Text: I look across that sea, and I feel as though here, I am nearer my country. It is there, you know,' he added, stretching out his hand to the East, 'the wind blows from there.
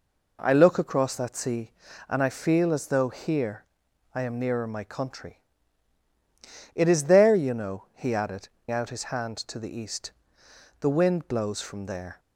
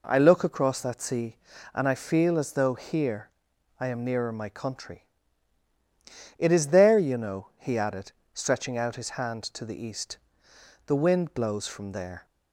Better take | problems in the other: second | skips "stretching"; at 8.5 s

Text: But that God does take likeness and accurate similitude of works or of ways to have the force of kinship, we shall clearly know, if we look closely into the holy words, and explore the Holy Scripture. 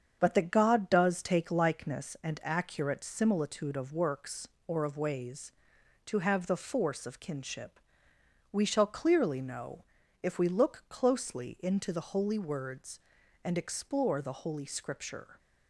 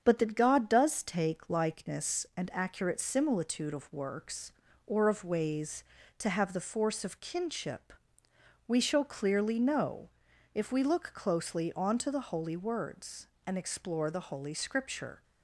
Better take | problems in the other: first | starts louder than the rest; strong; until 1.0 s; 7.5 dB; strong in the first // says "onto" for "into"; at 11.7 s

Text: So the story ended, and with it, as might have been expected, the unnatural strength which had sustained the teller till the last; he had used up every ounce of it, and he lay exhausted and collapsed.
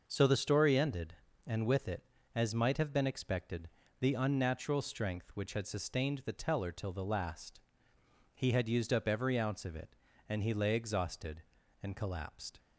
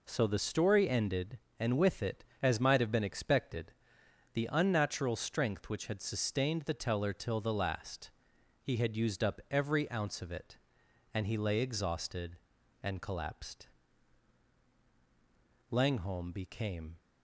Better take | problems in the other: first | goes on to say "Langholm became"; noticeable; from 15.7 s on; 1.2 s long

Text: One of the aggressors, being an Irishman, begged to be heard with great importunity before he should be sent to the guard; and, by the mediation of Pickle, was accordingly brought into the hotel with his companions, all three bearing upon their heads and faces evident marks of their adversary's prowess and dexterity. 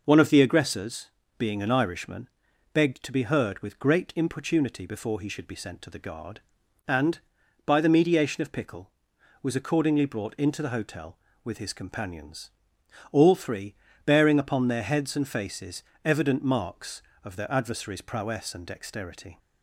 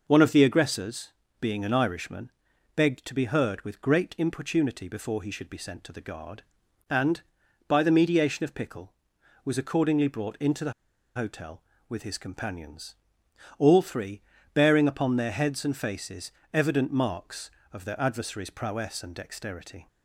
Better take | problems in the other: first | pauses between "the" and "hotel"; at 10.7 s; 0.43 s long // pauses between "three" and "bearing"; slight; at 14.2 s; 0.32 s long; slight in the first // pauses between "faces" and "evident"; slight; at 16.3 s; 0.22 s long; slight in the first

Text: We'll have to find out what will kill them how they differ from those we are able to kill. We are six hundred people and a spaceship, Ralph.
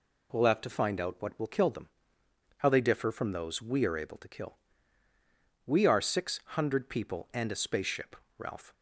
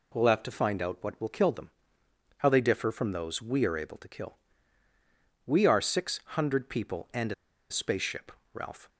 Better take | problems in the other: first | pauses between "them" and "how"; noticeable; at 1.7 s; 0.68 s long; noticeable in the first // pauses between "a" and "spaceship"; at 7.3 s; 0.37 s long

